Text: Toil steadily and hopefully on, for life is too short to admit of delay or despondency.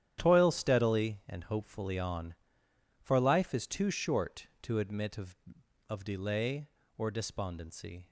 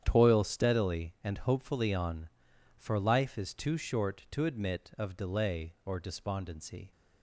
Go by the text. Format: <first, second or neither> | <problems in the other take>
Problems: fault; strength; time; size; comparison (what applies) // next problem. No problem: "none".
second | starts louder than the rest; strong; until 1.2 s; 10.5 dB; strong in the second // says "of" twice; at 5.8 s